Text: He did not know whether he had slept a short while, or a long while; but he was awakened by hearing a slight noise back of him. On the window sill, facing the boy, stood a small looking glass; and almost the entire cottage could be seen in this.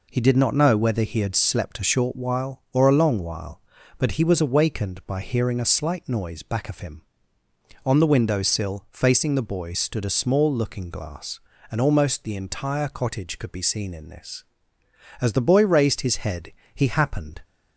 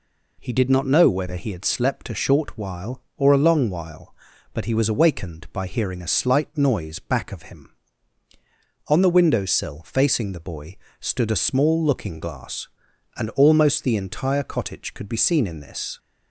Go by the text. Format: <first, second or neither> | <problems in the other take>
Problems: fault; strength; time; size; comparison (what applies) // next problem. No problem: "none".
second | goes on to say "As the boy raised his head he happened"; strong; from 15.2 s on; 2.2 s long